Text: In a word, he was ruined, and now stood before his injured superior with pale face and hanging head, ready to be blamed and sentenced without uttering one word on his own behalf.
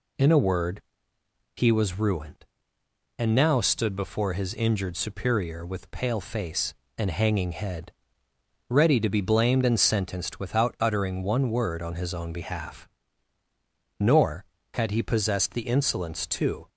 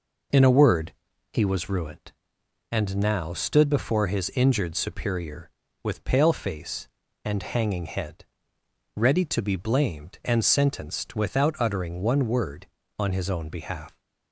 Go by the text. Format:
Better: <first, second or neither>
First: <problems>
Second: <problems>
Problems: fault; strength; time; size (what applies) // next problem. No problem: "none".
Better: second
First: goes on to say "Nor had he possessed the insolence to"; strong; from 13.9 s on; 2.7 s long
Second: none